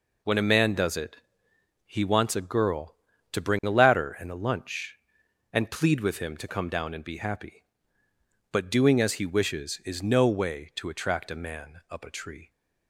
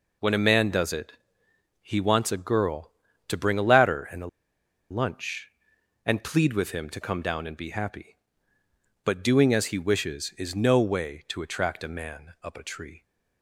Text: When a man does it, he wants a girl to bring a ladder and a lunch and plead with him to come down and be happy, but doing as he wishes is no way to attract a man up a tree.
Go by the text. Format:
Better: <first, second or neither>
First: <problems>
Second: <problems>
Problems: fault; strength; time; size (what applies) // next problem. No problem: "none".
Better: first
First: none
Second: pauses between "a" and "lunch"; noticeable; at 4.2 s; 0.63 s long